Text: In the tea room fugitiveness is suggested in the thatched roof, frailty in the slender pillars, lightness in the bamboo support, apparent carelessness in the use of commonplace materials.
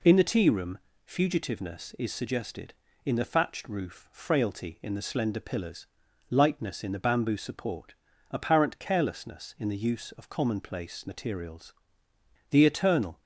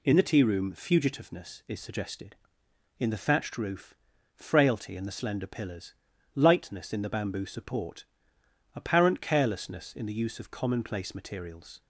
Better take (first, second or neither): second